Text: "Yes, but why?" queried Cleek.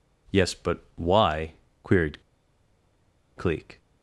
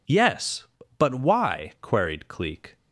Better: second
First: pauses between "queried" and "Cleek"; at 2.2 s; 1.1 s long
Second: none

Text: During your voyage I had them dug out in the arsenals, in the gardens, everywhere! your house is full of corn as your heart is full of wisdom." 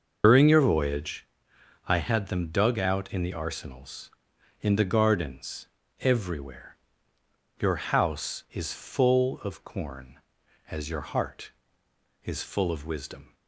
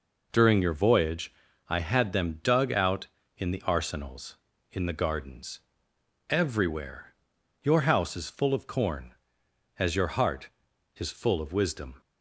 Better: second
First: loses the start of "During"; at 0.2 s; 95 ms // starts louder than the rest; noticeable; until 1.2 s; 6 dB // pauses between "voyage" and "I"; noticeable; at 1.2 s; 0.62 s long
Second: pauses between "voyage" and "I"; slight; at 1.3 s; 0.34 s long

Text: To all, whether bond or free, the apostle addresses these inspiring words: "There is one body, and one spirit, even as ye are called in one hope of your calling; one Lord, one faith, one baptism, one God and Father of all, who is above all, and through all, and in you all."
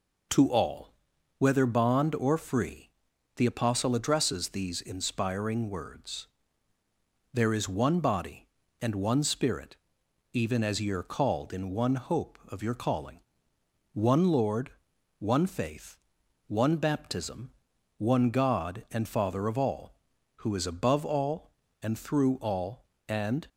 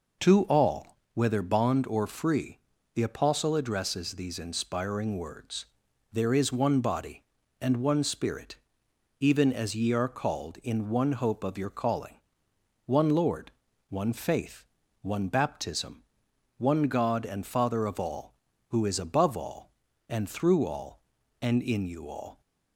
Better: second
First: stops before "in you all"; at 23.4 s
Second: none

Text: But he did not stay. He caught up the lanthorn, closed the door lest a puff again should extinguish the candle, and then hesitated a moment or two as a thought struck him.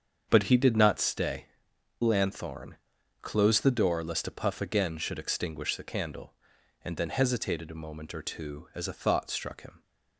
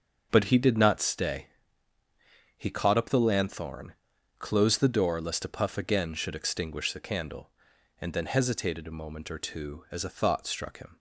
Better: second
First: starts louder than the rest; strong; until 1.3 s; 7.5 dB // skips "He caught up the"; at 1.7 s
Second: starts louder than the rest; until 1.3 s; 6.5 dB

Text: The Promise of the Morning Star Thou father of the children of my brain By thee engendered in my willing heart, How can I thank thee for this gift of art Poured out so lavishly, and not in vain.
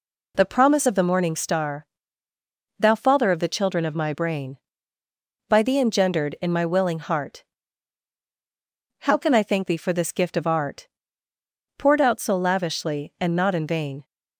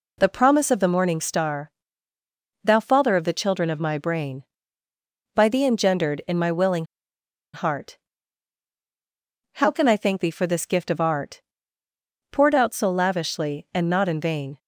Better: first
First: pauses between "Star" and "Thou"; noticeable; at 1.8 s; 0.94 s long // pauses between "art" and "Poured"; noticeable; at 10.8 s; 0.90 s long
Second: pauses between "Star" and "Thou"; noticeable; at 1.7 s; 0.94 s long // pauses between "willing" and "heart"; noticeable; at 6.8 s; 0.70 s long // pauses between "art" and "Poured"; noticeable; at 11.4 s; 0.90 s long

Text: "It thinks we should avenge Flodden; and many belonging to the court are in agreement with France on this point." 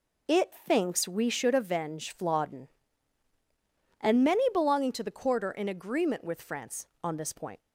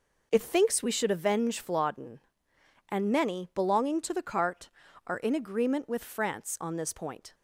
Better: first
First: none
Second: says "cart" for "court"; at 4.2 s

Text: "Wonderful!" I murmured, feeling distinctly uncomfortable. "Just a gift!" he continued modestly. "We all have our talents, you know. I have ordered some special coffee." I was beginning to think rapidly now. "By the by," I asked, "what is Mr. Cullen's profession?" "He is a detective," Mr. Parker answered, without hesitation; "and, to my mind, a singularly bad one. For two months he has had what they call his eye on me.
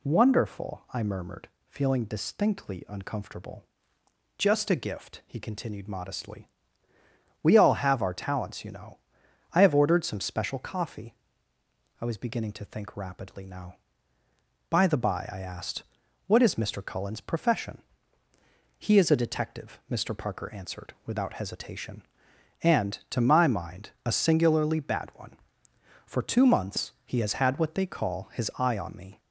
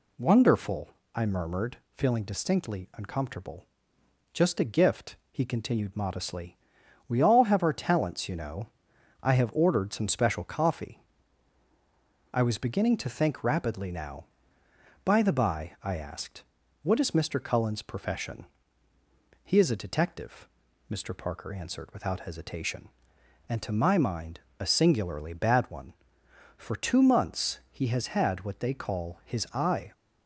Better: first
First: none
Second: stops before "on me"; at 29.9 s

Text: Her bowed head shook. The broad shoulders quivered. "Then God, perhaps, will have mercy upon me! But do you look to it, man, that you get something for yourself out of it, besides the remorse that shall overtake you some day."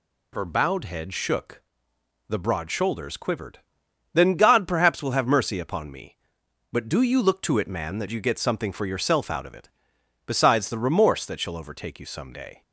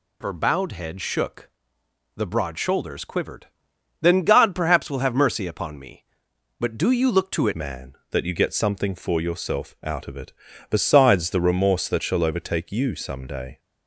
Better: first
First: none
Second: changes voice at "man"; from 7.5 s on; 6.0 s long

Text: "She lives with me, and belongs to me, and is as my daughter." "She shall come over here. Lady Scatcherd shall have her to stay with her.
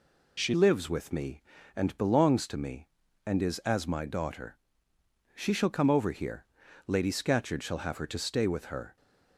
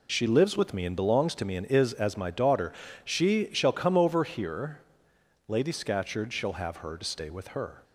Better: second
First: changes voice at "lives"; from 0.5 s on; 8.4 s long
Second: none

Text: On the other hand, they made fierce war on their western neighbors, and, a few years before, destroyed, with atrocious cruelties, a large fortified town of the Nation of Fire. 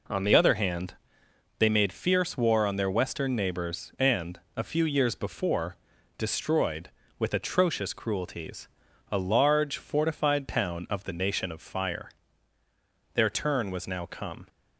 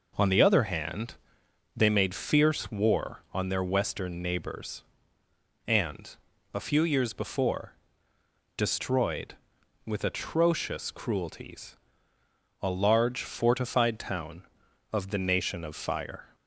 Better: second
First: goes on to say "Their turn was now come"; from 13.1 s on; 1.3 s long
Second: none

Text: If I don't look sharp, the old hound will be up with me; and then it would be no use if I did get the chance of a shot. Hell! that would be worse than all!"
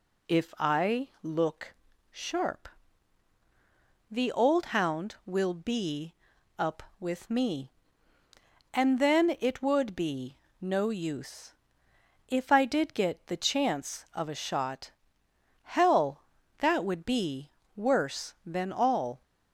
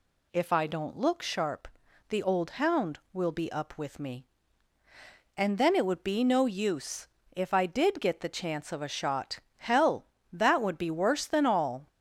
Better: second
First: skips "don't"; at 1.1 s // pauses between "look" and "sharp"; slight; at 1.7 s; 0.34 s long // pauses between "be" and "up"; at 6.1 s; 0.42 s long // pauses between "be" and "no"; slight; at 10.3 s; 0.24 s long // pauses between "use" and "if"; noticeable; at 11.5 s; 0.74 s long // pauses between "be" and "worse"; slight; at 17.5 s; 0.24 s long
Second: pauses between "use" and "if"; slight; at 7.0 s; 0.28 s long

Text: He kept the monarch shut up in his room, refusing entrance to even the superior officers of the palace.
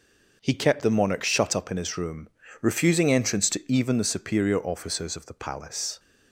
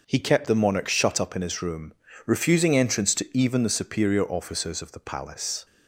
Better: neither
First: none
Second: none

